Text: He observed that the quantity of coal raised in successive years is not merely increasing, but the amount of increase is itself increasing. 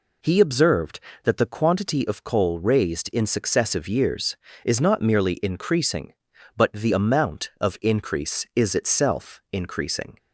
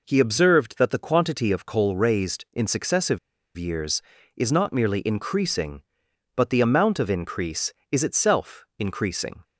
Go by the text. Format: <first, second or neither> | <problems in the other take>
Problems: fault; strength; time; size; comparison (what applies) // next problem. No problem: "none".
first | pauses between "successive" and "years"; at 3.1 s; 0.38 s long